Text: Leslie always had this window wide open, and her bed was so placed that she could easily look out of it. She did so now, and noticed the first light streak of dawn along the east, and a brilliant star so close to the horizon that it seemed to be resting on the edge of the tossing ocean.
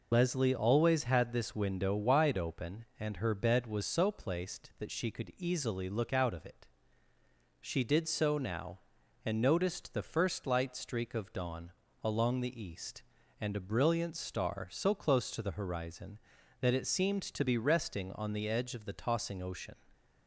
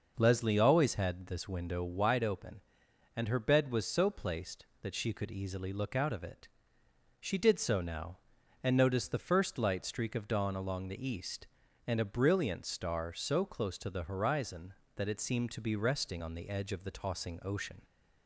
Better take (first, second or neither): second